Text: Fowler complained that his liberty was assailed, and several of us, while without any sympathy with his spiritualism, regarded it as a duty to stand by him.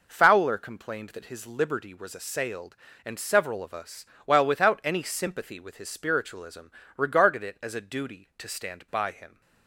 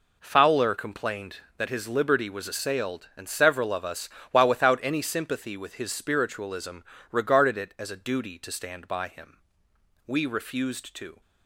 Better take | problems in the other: first | goes on to say "We refused to"; noticeable; from 10.0 s on; 1.1 s long

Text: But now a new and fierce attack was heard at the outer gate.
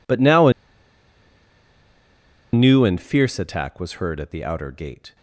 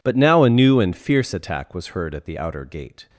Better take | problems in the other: second | pauses between "a" and "new"; strong; at 0.5 s; 2.0 s long

